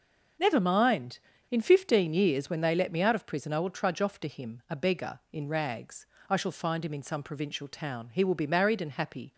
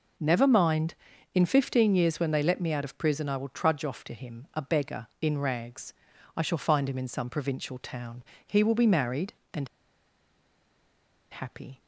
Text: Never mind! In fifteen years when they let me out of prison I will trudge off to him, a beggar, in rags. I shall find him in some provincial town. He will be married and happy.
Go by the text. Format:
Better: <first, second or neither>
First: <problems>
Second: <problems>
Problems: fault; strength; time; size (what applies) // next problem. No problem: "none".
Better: first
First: none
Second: pauses between "and" and "happy"; strong; at 9.6 s; 1.6 s long